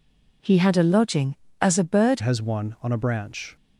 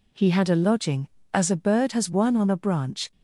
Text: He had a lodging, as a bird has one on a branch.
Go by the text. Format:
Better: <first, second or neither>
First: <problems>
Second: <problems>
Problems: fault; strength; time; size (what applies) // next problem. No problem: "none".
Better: second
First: changes voice at "has"; from 2.2 s on; 1.3 s long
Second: none